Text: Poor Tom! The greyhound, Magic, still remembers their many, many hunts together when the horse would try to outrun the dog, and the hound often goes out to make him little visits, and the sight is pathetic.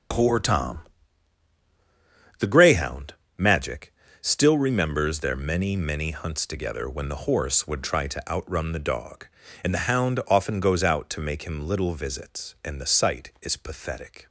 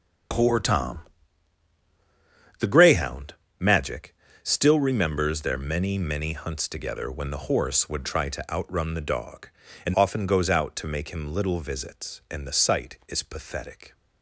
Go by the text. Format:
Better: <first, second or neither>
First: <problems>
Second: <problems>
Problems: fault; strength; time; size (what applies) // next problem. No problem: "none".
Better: first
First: starts louder than the rest; strong; until 2.7 s; 8 dB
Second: starts louder than the rest; strong; until 2.9 s; 8 dB // skips "the hound"; at 9.9 s